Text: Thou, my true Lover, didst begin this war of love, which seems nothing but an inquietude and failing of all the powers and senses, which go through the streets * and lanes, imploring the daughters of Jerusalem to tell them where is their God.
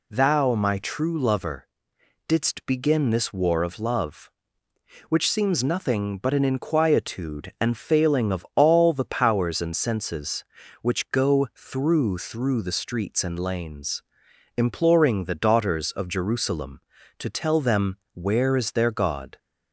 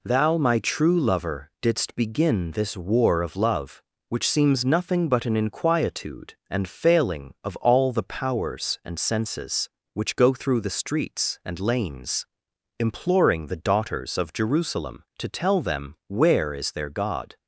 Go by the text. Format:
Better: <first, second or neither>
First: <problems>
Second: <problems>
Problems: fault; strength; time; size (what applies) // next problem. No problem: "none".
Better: second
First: says "through" twice; at 12.1 s // pauses between "them" and "where"; slight; at 17.9 s; 0.16 s long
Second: none